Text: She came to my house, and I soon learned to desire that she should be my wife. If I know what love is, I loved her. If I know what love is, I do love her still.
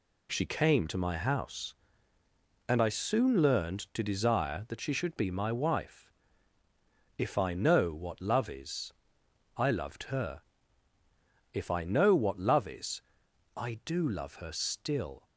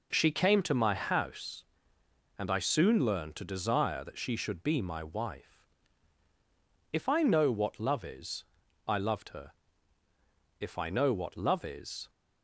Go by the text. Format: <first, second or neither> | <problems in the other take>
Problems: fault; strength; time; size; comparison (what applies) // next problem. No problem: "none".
first | stops before "I do love her still"; at 12.0 s